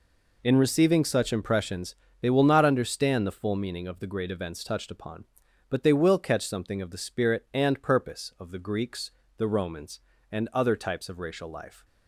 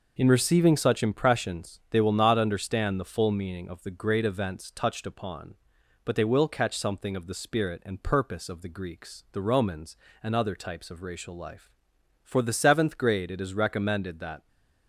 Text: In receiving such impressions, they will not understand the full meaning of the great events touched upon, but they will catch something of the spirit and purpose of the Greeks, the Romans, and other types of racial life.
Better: first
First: none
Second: goes on to say "For the seventh grade it is recommended that"; strong; from 12.2 s on; 2.2 s long

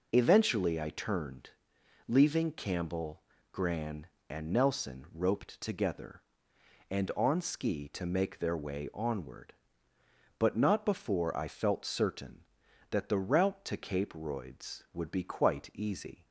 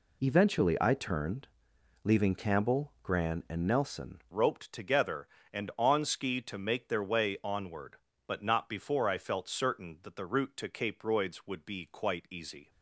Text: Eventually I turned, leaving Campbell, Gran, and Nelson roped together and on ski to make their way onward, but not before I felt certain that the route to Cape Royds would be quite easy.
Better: first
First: none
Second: changes voice at "roped"; from 4.3 s on; 8.4 s long

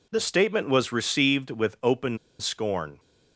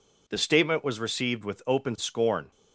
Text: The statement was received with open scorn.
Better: second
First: pauses between "open" and "scorn"; slight; at 2.1 s; 0.21 s long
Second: none

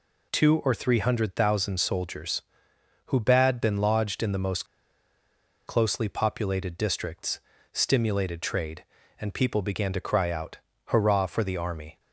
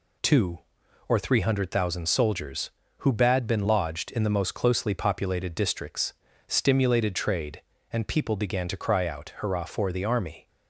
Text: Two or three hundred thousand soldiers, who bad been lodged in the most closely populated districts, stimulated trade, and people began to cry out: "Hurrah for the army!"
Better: second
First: pauses between "most" and "closely"; at 4.6 s; 1.0 s long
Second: none

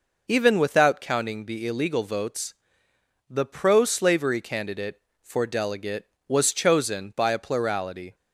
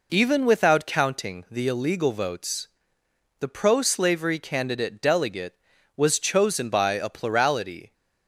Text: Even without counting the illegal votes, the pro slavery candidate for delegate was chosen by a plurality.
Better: first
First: none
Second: skips "for"; at 5.0 s

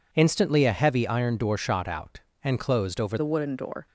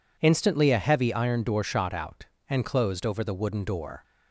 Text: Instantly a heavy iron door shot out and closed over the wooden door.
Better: second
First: changes voice at "the"; from 3.1 s on; 0.7 s long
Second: none

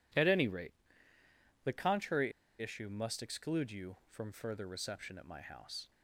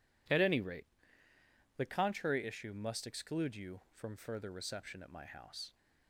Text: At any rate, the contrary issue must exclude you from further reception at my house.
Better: second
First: pauses between "contrary" and "issue"; slight; at 2.3 s; 0.30 s long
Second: none

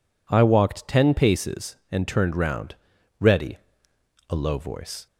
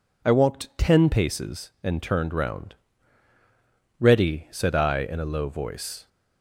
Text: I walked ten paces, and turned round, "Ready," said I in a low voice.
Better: second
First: skips "said I in"; at 3.9 s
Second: none

